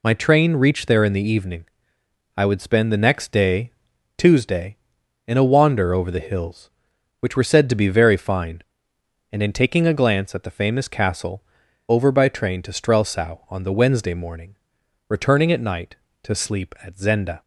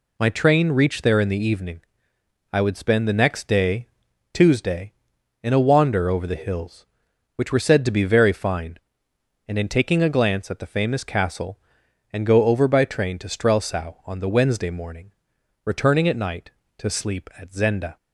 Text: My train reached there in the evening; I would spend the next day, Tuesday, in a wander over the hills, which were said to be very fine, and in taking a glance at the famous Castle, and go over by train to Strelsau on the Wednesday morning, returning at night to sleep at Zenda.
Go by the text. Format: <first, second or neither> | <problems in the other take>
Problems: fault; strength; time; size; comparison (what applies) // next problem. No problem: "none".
second | skips "and go"; at 11.6 s